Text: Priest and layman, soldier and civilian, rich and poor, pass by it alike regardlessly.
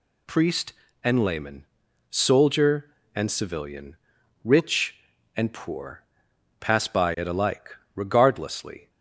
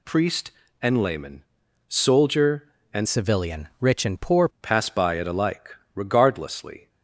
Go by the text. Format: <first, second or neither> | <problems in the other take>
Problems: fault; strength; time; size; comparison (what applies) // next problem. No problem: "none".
first | changes voice from "civilian" to "poor"; from 3.0 to 4.4 s; 1.4 s long // pauses between "alike" and "regardlessly"; slight; at 5.7 s; 0.18 s long; slight in the first